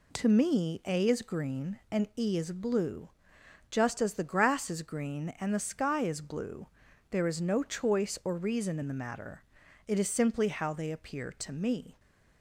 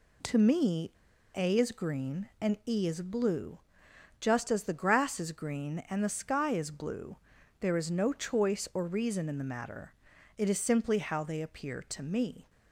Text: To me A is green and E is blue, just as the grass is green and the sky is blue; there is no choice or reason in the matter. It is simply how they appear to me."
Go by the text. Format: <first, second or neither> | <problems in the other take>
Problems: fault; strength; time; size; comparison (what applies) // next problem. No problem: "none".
first | pauses between "me" and "A"; at 0.9 s; 0.44 s long